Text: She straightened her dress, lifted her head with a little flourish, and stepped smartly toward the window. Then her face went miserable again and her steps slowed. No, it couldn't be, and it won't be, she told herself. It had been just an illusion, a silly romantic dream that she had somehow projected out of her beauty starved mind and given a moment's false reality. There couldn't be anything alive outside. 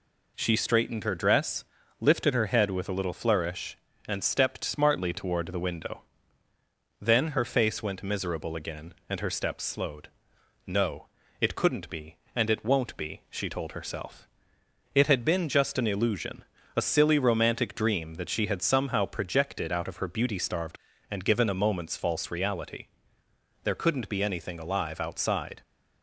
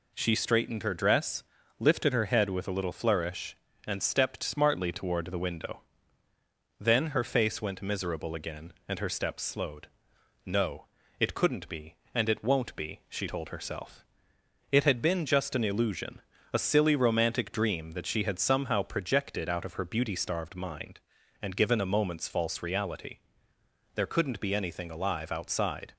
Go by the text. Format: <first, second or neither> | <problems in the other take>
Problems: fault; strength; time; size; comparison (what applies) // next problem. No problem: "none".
second | skips "mind"; at 20.9 s